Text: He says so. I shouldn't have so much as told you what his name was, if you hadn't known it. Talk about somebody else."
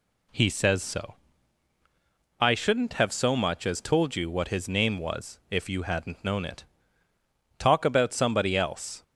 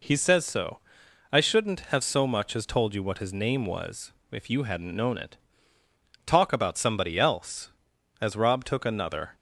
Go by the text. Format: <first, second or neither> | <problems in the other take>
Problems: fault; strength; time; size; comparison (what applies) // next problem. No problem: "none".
first | goes on to say "As Rob took another"; noticeable; from 8.2 s on; 1.1 s long